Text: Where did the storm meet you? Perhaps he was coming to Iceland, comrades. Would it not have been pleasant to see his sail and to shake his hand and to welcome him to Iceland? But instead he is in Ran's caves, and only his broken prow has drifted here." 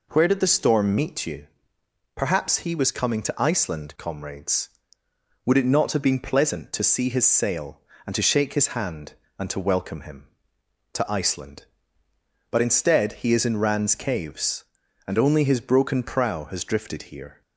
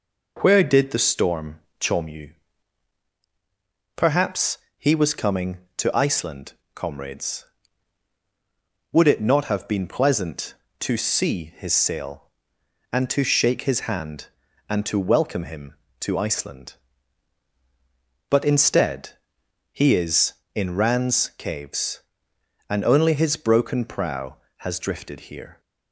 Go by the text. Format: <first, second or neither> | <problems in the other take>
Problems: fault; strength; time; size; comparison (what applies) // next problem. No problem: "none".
first | says "chom" for "meet"; at 1.7 s // pauses between "Perhaps" and "he"; slight; at 4.5 s; 0.18 s long // pauses between "instead" and "he"; noticeable; at 19.1 s; 0.60 s long